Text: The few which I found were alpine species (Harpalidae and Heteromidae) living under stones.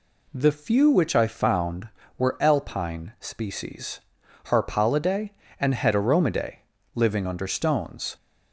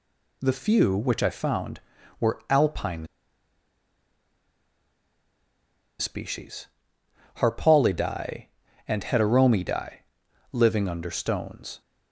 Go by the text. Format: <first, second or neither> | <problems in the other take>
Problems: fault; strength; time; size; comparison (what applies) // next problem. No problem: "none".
first | pauses between "alpine" and "species"; strong; at 3.0 s; 2.9 s long